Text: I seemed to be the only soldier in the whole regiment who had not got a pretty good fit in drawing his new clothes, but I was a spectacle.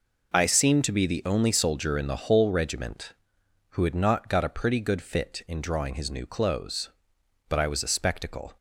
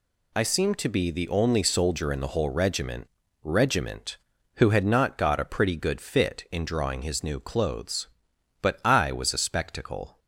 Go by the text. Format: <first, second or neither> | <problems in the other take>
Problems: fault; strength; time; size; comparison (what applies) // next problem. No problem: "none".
first | says "regiment" twice; at 3.4 s